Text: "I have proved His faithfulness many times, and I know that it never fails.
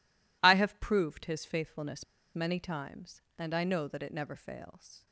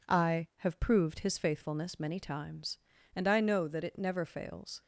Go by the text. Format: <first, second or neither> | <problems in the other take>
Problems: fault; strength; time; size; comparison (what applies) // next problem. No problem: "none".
second | pauses between "faithfulness" and "many"; slight; at 2.0 s; 0.31 s long